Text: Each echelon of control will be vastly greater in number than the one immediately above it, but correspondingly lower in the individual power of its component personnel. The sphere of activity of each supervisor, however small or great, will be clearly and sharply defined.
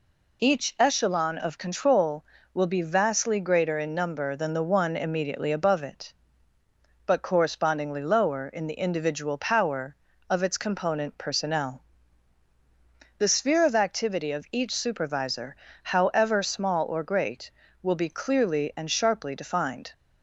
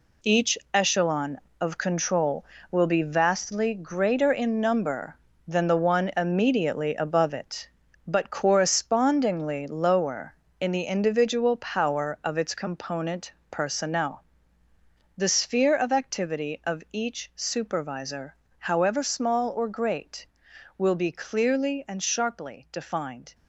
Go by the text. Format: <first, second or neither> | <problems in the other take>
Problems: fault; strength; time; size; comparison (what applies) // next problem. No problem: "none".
first | gets quieter; strong; throughout; 9 dB // pauses between "Each" and "echelon"; slight; at 0.5 s; 0.16 s long // pauses between "component" and "personnel"; slight; at 13.3 s; 0.18 s long